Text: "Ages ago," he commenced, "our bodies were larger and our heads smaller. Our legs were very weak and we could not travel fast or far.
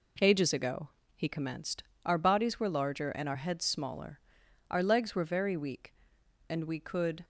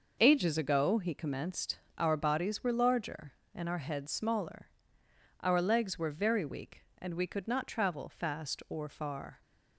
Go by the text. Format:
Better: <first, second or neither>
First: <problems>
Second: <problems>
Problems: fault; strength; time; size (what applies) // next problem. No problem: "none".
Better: second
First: stops before "not travel fast or far"; at 7.2 s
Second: none